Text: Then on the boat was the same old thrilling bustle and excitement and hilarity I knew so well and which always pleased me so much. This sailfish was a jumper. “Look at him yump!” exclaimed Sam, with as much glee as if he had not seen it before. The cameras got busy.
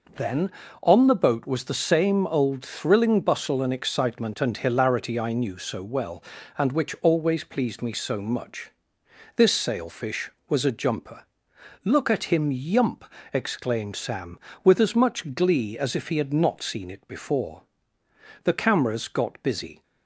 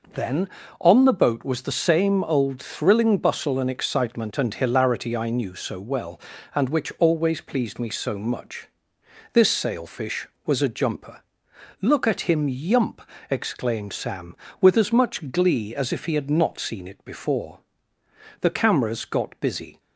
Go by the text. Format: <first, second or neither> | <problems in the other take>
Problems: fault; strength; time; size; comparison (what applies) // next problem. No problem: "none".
neither | none